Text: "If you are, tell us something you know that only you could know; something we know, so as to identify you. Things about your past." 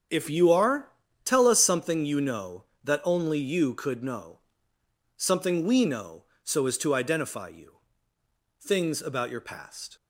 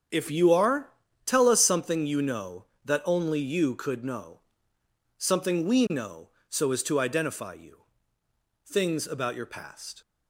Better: neither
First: starts louder than the rest; strong; until 1.4 s; 7 dB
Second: starts louder than the rest; strong; until 1.4 s; 7 dB

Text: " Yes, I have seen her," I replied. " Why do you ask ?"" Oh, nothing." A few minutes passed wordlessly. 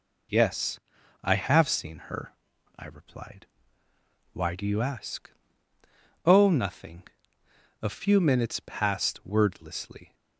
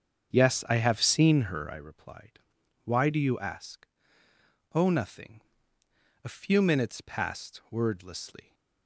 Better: first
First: none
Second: starts louder than the rest; strong; until 1.9 s; 8 dB

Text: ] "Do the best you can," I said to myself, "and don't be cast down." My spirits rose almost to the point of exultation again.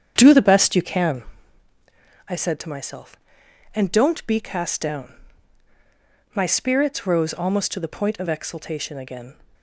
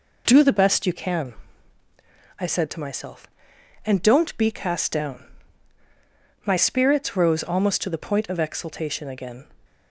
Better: second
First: starts louder than the rest; strong; until 1.5 s; 8.5 dB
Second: none

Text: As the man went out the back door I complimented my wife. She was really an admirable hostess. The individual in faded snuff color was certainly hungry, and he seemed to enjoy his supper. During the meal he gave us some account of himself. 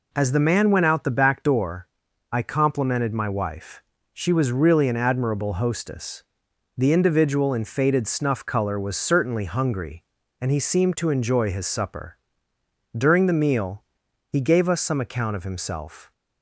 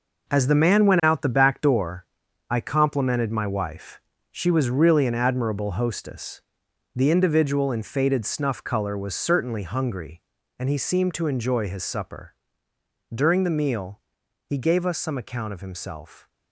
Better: first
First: pauses between "door" and "I"; noticeable; at 1.8 s; 0.46 s long // pauses between "meal" and "he"; noticeable; at 13.8 s; 0.46 s long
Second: gets quieter; strong; throughout; 9.5 dB // pauses between "door" and "I"; noticeable; at 2.0 s; 0.46 s long // pauses between "meal" and "he"; noticeable; at 13.9 s; 0.46 s long

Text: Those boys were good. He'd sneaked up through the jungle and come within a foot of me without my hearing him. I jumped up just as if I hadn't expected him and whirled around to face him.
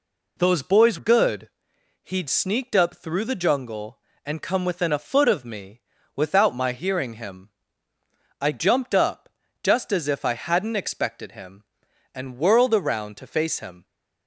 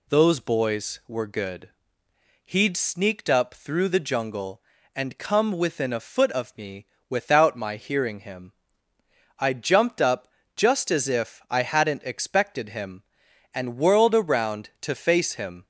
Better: second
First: skips "were"; at 0.9 s // pauses between "me" and "without"; slight; at 5.8 s; 0.34 s long // pauses between "up" and "just"; slight; at 9.2 s; 0.32 s long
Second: pauses between "me" and "without"; slight; at 6.8 s; 0.22 s long // pauses between "up" and "just"; slight; at 10.2 s; 0.28 s long

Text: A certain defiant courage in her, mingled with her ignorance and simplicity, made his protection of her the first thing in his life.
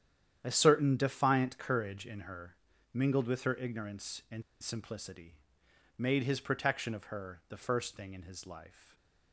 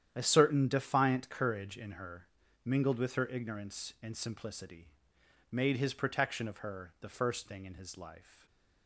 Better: second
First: starts louder than the rest; strong; until 1.4 s; 10 dB // pauses between "and" and "simplicity"; slight; at 4.4 s; 0.21 s long // stays silent after the last word; slight; from 8.6 s on; 0.7 s long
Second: starts louder than the rest; strong; until 1.1 s; 10 dB // stays silent after the last word; slight; from 8.2 s on; 0.6 s long

